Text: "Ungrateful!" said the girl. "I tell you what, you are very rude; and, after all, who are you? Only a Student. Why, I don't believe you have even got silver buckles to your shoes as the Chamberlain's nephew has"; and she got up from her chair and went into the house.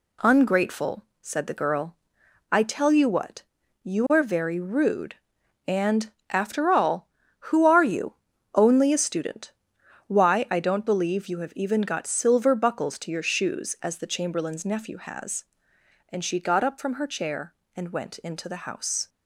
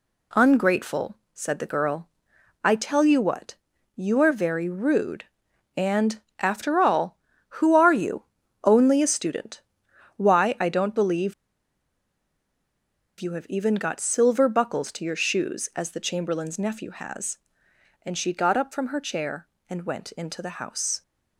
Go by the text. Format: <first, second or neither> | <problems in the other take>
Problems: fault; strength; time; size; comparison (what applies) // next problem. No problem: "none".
first | pauses between "believe" and "you"; strong; at 11.3 s; 1.8 s long